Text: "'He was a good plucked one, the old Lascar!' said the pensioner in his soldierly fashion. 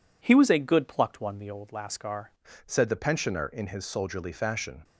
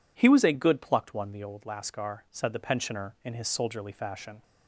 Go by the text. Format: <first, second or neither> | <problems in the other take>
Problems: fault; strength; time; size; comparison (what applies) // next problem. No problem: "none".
second | changes voice at "said"; from 2.6 s on; 2.2 s long